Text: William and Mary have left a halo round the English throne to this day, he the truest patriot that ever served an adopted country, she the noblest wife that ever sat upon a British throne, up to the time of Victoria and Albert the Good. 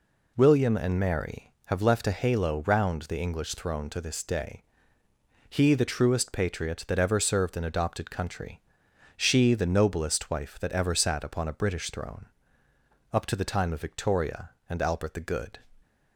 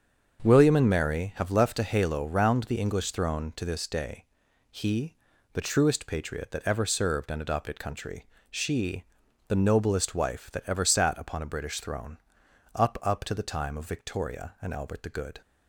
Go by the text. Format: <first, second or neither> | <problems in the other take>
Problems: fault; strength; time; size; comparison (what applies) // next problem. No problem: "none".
first | starts louder than the rest; until 1.4 s; 7 dB // pauses between "he" and "the"; at 5.1 s; 0.38 s long // pauses between "she" and "the"; noticeable; at 9.0 s; 0.46 s long // says "up" twice; at 13.0 s